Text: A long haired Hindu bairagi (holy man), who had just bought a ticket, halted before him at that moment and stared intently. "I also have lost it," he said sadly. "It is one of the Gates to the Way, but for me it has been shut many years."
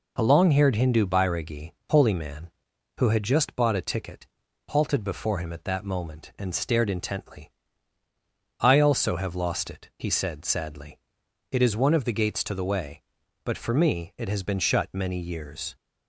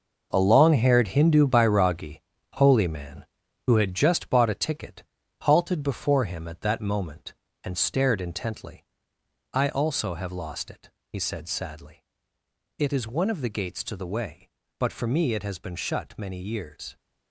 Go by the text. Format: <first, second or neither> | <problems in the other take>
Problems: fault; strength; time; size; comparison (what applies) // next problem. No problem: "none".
first | gets quieter; strong; throughout; 10.5 dB